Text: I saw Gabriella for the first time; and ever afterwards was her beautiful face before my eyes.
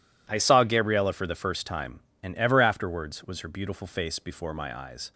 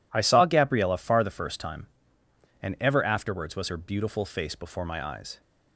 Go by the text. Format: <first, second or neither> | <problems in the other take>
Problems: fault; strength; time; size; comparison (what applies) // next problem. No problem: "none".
first | says "far" for "for"; at 0.9 s